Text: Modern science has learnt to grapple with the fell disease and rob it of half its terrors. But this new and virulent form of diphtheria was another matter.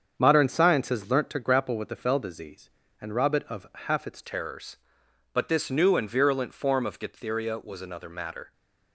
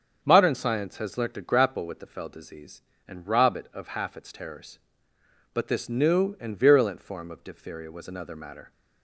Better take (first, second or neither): second